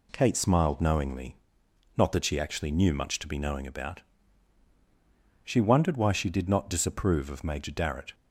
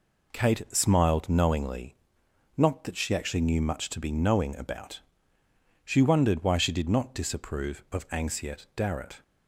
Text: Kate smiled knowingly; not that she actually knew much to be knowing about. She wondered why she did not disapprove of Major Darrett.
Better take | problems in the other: first | says "Anxiet" for "Major"; at 8.1 s

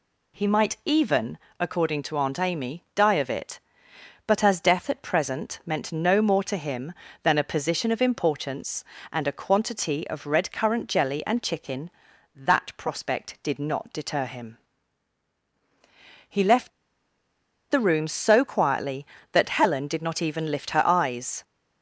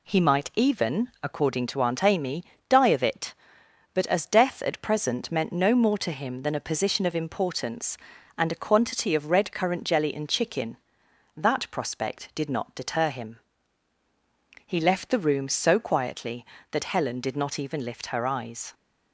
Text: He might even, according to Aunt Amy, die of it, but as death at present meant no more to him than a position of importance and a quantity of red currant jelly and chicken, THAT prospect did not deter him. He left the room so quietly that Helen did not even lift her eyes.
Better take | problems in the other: second | pauses between "left" and "the"; at 16.6 s; 1.0 s long

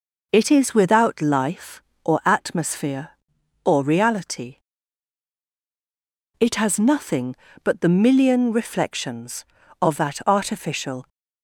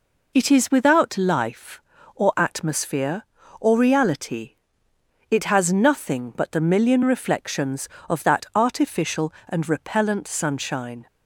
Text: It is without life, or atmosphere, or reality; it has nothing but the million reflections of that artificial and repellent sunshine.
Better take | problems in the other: second | stops before "and repellent sunshine"; at 11.0 s

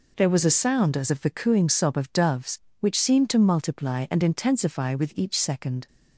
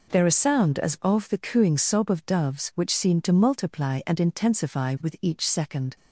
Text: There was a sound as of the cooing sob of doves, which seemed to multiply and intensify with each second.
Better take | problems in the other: first | skips "was"; at 0.2 s

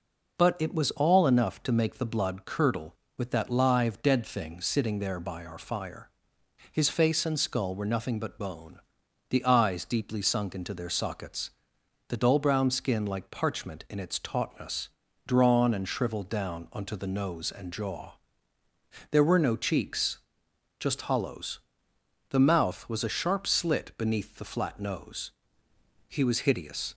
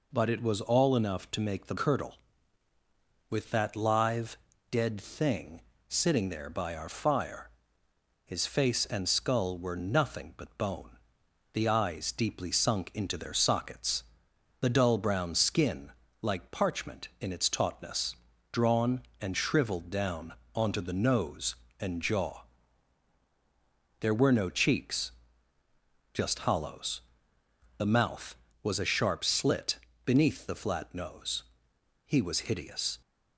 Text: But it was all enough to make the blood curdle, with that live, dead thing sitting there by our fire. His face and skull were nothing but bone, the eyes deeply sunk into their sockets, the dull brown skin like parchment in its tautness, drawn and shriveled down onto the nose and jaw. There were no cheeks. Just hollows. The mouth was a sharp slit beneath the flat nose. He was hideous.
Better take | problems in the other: first | skips "blood"; at 1.7 s // pauses between "thing" and "sitting"; slight; at 5.6 s; 0.26 s long // pauses between "skin" and "like"; slight; at 15.9 s; 0.28 s long // pauses between "down" and "onto"; slight; at 20.3 s; 0.20 s long // pauses between "slit" and "beneath"; slight; at 29.7 s; 0.28 s long

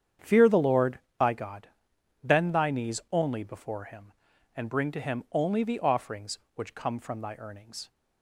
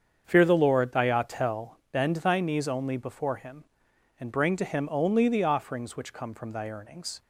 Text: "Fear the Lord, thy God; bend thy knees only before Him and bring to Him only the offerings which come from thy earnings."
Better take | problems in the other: first | starts louder than the rest; strong; until 1.2 s; 7.5 dB; strong in the first // says "Atel" for "God"; at 1.0 s

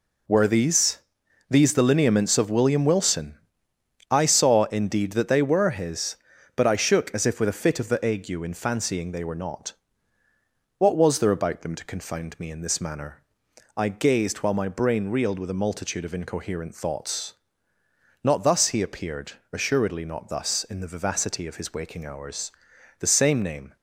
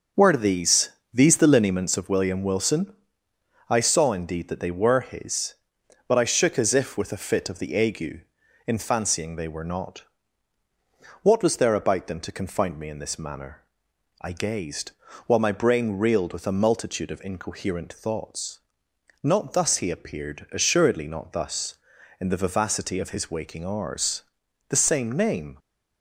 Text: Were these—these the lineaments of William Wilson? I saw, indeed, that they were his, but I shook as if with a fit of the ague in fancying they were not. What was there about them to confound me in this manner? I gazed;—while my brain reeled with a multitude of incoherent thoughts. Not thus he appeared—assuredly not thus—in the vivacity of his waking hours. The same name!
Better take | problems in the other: first | starts louder than the rest; noticeable; until 1.8 s; 6 dB

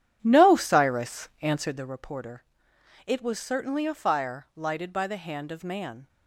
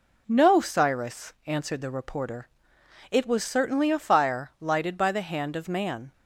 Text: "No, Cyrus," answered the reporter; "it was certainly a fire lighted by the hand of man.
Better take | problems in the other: second | starts louder than the rest; strong; until 1.9 s; 10.5 dB

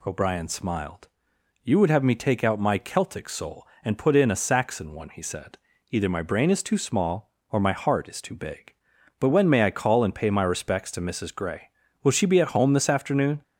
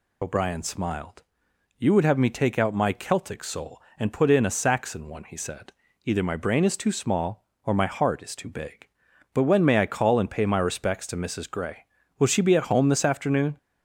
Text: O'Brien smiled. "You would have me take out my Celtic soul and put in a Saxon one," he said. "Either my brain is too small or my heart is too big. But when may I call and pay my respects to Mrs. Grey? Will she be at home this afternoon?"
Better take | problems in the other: first | loses the start of "O'Brien"; at 0.2 s; 45 ms

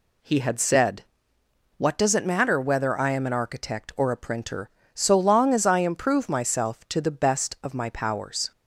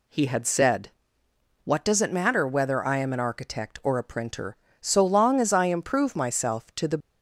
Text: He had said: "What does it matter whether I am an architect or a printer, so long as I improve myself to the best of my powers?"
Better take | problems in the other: first | stops before "best of my powers"; at 6.9 s

